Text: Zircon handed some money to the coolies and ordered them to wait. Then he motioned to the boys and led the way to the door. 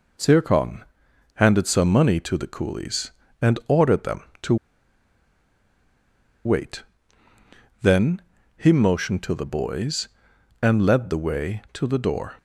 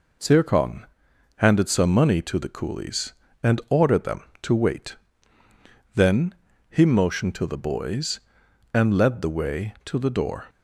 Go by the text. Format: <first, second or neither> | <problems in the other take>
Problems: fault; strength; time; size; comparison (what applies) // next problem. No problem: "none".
second | pauses between "Zircon" and "handed"; noticeable; at 0.8 s; 0.52 s long; noticeable in the second // pauses between "to" and "wait"; strong; at 4.5 s; 1.9 s long // pauses between "Then" and "he"; slight; at 8.2 s; 0.36 s long; slight in the second